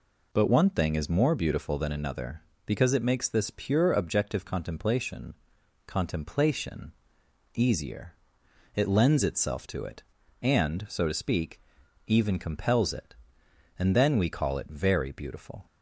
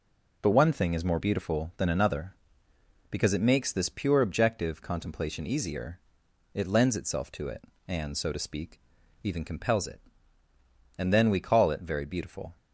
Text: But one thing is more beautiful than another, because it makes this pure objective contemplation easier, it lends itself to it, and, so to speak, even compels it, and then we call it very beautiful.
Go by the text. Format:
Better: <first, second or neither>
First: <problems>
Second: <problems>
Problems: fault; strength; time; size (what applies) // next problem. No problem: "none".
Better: second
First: says "contemplation" twice; at 5.8 s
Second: none